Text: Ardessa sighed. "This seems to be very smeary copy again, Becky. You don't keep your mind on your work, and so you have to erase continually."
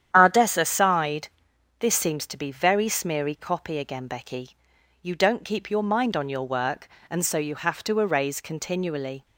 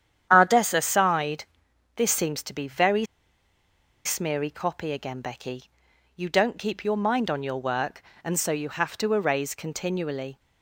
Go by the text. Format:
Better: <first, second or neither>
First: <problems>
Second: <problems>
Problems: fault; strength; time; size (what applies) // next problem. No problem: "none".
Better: first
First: starts louder than the rest; strong; until 1.1 s; 9.5 dB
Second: starts louder than the rest; strong; until 1.3 s; 9.5 dB // pauses between "very" and "smeary"; at 3.0 s; 0.99 s long